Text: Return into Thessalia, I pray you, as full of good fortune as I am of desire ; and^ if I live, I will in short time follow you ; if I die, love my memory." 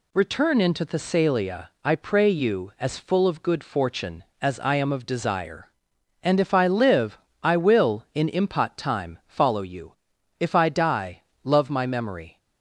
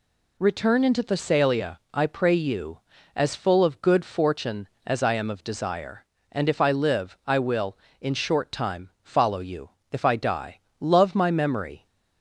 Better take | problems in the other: second | says "impot" for "short"; at 8.2 s

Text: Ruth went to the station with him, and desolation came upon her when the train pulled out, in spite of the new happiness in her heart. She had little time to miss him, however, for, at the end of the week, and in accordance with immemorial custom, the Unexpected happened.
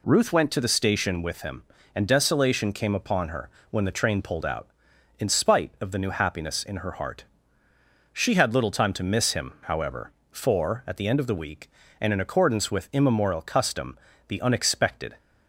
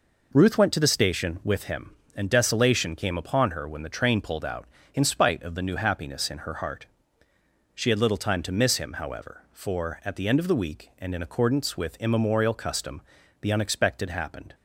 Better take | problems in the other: second | pauses between "her" and "when"; slight; at 3.4 s; 0.22 s long // stops before "happened"; at 15.1 s

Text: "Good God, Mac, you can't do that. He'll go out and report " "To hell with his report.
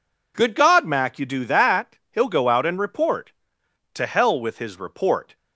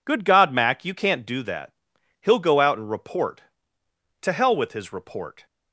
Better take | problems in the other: second | skips "can't"; at 1.2 s

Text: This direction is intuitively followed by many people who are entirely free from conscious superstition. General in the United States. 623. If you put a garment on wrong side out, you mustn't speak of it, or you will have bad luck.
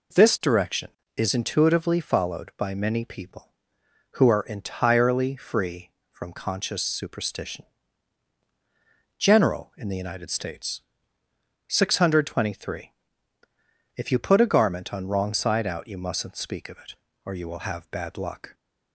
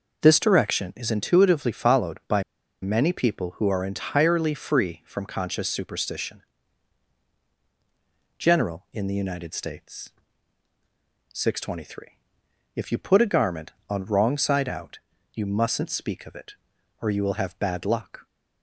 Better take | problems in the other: first | pauses between "by" and "many"; at 2.4 s; 0.39 s long

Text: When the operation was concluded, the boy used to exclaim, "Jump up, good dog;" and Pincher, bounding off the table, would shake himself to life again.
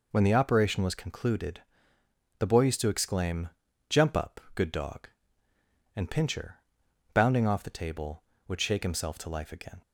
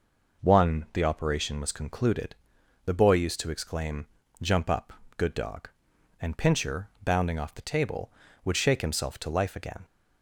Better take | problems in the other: first | says "One" for "When"; at 0.4 s

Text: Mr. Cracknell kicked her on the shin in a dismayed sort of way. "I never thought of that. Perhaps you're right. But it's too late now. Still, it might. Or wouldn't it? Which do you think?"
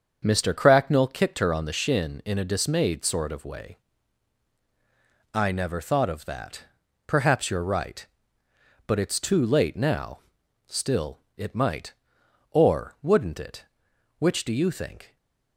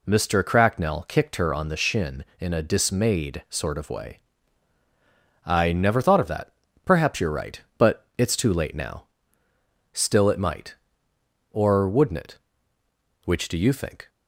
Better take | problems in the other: second | starts louder than the rest; until 1.3 s; 7 dB // stays silent after the last word; slight; from 15.0 s on; 0.5 s long

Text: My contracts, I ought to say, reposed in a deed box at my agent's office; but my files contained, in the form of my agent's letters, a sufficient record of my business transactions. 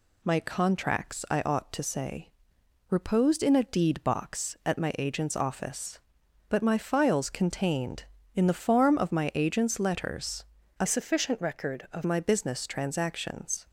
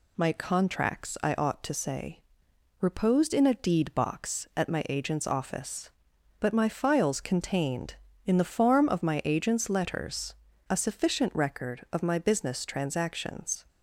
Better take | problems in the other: second | changes voice from "sufficient" to "of"; from 10.8 to 12.0 s; 1.2 s long

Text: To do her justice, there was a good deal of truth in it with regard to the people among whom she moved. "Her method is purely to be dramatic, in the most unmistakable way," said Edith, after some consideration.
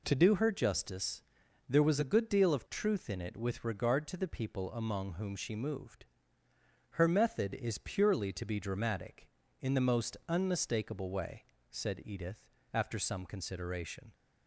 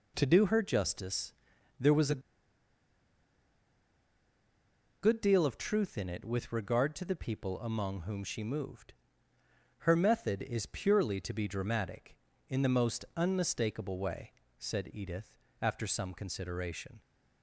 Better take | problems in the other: first | pauses between "a" and "good"; strong; at 2.2 s; 2.8 s long

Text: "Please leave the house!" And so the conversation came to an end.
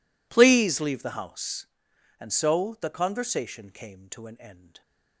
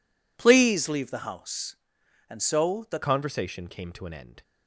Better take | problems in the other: first | changes voice at "conversation"; from 3.0 s on; 1.4 s long

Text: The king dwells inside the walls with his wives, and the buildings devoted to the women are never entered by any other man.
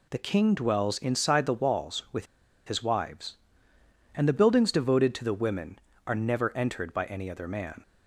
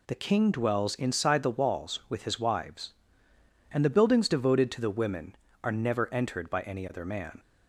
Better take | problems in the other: second | pauses between "with" and "his"; at 2.2 s; 0.42 s long

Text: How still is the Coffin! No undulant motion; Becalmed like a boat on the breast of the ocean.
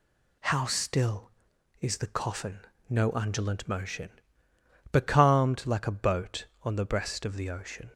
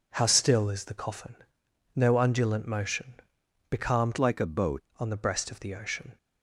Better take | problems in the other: first | changes voice from "like" to "boat"; from 4.1 to 4.8 s; 0.7 s long

